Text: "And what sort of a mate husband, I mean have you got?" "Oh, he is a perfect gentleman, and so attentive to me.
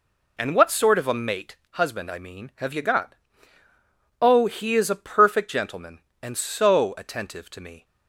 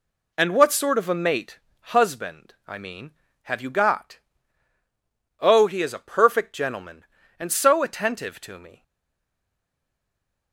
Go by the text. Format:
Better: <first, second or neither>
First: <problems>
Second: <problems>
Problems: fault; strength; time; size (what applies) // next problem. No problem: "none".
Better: first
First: pauses between "mate" and "husband"; slight; at 1.5 s; 0.16 s long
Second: pauses between "mate" and "husband"; slight; at 1.5 s; 0.34 s long // stays silent after the last word; noticeable; from 8.8 s on; 1.7 s long